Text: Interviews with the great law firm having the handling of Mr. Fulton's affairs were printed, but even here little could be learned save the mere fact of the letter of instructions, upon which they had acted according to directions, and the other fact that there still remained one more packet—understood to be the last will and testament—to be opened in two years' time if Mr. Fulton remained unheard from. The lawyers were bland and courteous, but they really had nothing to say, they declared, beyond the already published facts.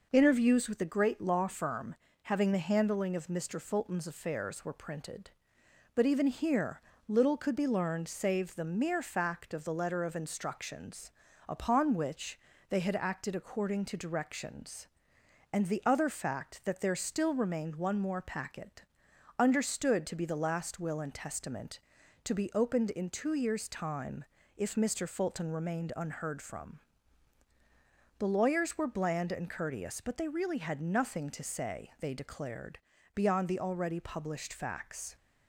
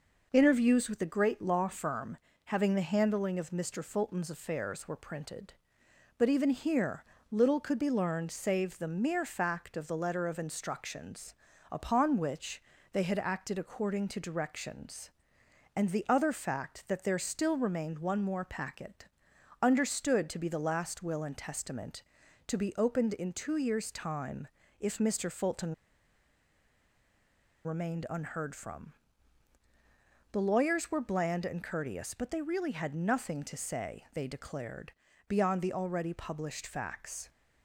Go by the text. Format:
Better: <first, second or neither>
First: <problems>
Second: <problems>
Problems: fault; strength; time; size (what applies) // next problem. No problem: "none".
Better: first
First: pauses between "firm" and "having"; slight; at 1.9 s; 0.28 s long // pauses between "here" and "little"; slight; at 6.7 s; 0.28 s long // pauses between "which" and "they"; slight; at 12.3 s; 0.32 s long // pauses between "time" and "if"; slight; at 24.2 s; 0.34 s long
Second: pauses between "firm" and "having"; slight; at 2.1 s; 0.28 s long // pauses between "here" and "little"; slight; at 7.0 s; 0.28 s long // pauses between "which" and "they"; slight; at 12.6 s; 0.32 s long // pauses between "time" and "if"; slight; at 24.4 s; 0.34 s long // pauses between "Fulton" and "remained"; strong; at 25.7 s; 1.9 s long